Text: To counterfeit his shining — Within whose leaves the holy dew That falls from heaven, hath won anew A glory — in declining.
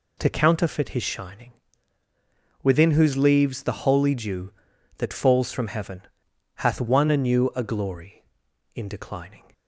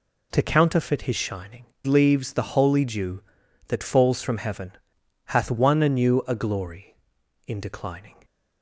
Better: first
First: none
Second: skips "Within whose"; at 1.7 s

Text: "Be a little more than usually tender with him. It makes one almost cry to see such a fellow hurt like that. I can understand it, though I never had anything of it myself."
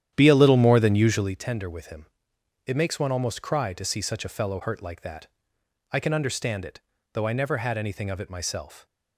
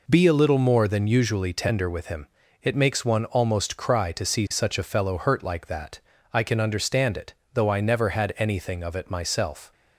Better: second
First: starts louder than the rest; strong; until 1.4 s; 10.5 dB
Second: none

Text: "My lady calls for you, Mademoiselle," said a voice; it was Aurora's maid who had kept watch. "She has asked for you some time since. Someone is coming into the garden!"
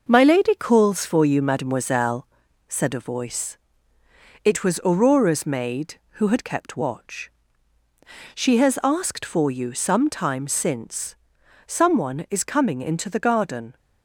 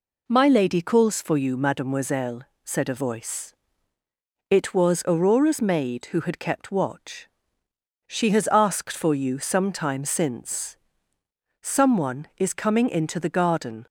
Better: second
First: gets quieter; noticeable; throughout; 5.5 dB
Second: none

